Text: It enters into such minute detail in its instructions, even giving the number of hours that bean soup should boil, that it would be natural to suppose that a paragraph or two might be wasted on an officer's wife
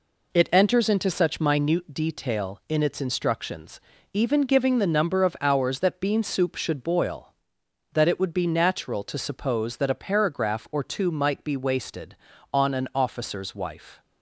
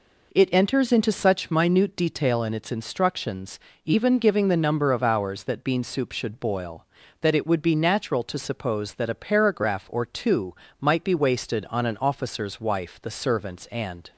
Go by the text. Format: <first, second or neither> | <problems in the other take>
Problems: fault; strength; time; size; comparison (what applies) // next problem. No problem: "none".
first | pauses between "two" and "might"; slight; at 10.5 s; 0.26 s long // goes on to say "The servants and"; noticeable; from 13.0 s on; 1.1 s long